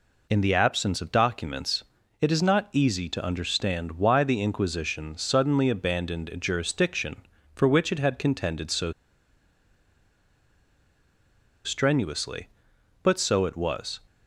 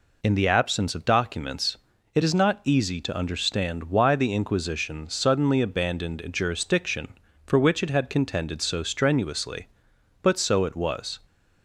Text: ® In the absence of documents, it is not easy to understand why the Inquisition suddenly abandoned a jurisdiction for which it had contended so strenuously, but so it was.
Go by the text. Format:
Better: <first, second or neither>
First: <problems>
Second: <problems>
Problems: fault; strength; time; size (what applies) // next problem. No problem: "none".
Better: second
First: pauses between "so" and "strenuously"; strong; at 8.9 s; 2.7 s long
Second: none